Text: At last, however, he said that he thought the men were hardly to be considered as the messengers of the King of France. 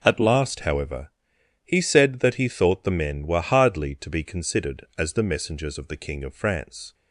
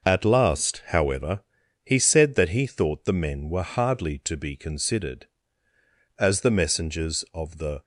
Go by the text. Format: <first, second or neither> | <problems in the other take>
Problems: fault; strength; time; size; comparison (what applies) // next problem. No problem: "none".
first | stops before "King of France"; at 7.8 s